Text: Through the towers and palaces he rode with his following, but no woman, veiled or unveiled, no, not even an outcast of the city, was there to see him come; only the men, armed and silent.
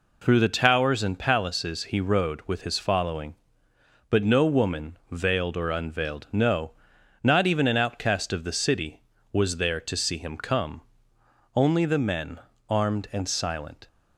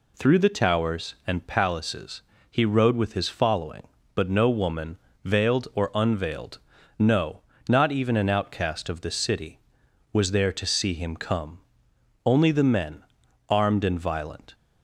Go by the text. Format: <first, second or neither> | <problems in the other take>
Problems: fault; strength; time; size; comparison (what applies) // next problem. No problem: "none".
first | pauses between "palaces" and "he"; slight; at 2.2 s; 0.28 s long // says "violent" for "silent"; at 13.9 s